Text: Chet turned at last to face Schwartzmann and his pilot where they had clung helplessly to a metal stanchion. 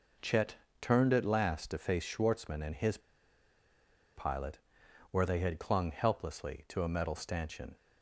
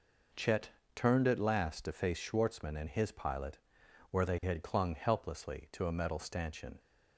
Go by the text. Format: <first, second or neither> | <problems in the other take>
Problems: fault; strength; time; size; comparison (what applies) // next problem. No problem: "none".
second | pauses between "Chet" and "turned"; slight; at 0.5 s; 0.24 s long; slight in the second // pauses between "his" and "pilot"; at 2.9 s; 1.1 s long // pauses between "pilot" and "where"; noticeable; at 4.5 s; 0.54 s long; noticeable in the second